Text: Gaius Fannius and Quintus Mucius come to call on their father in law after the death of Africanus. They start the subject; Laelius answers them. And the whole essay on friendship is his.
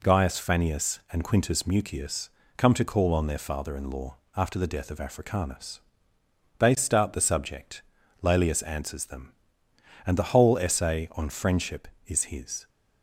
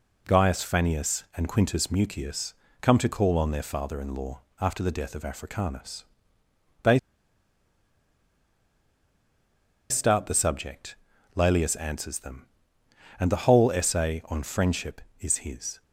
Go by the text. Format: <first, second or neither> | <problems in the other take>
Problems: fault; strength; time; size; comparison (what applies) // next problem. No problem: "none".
first | pauses between "Mucius" and "come"; slight; at 2.5 s; 0.26 s long; slight in the first // pauses between "law" and "after"; slight; at 4.4 s; 0.18 s long; slight in the first // pauses between "They" and "start"; strong; at 6.9 s; 2.9 s long